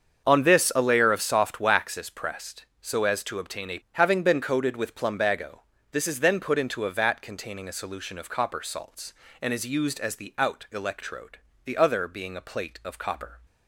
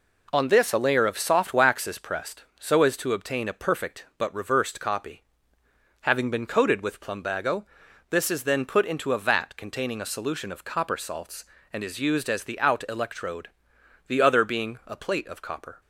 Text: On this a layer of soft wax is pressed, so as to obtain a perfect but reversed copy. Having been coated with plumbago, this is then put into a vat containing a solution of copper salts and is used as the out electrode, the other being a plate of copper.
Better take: second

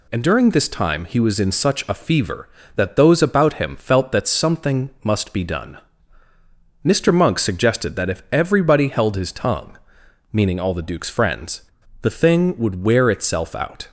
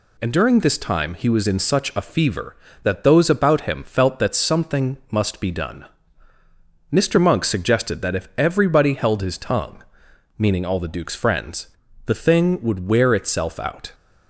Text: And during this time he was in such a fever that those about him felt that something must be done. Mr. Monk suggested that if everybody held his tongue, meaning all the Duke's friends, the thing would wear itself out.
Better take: neither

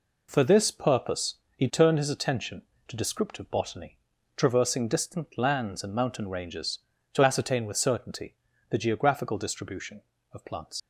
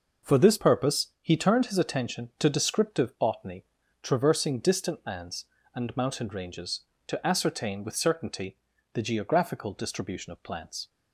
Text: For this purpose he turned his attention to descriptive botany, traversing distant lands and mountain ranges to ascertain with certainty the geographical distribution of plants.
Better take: second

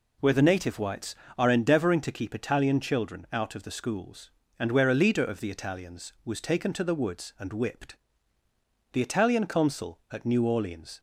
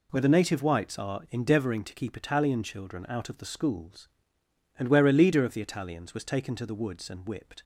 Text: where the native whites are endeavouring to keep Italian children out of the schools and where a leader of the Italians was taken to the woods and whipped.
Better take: second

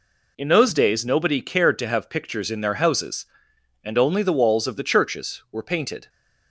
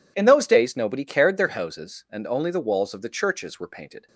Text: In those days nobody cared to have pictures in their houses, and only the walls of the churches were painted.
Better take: first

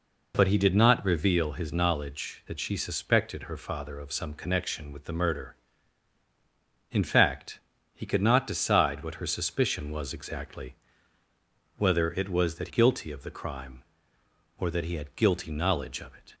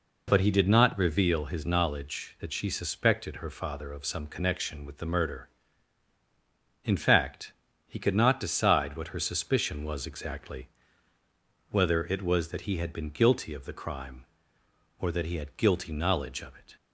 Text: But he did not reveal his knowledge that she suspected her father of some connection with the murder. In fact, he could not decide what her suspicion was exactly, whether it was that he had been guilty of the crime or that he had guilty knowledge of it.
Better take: second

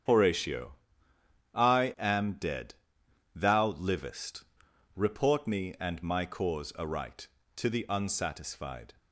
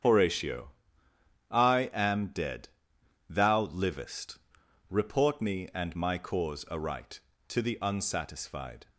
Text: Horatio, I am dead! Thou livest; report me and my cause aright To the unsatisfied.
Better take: neither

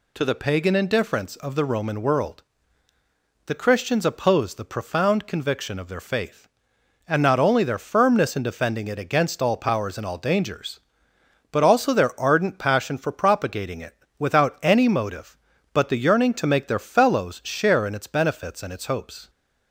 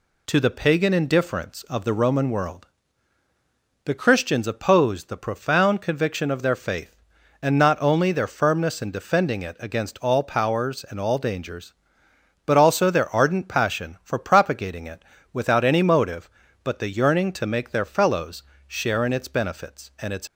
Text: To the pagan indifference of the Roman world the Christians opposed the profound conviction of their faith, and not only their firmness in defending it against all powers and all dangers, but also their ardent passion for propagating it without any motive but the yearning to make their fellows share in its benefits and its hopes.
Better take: first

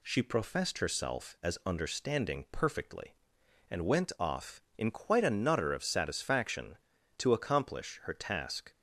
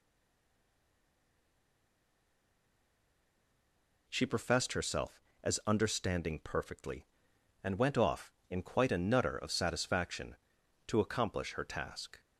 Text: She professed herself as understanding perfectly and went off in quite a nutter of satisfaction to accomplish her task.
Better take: first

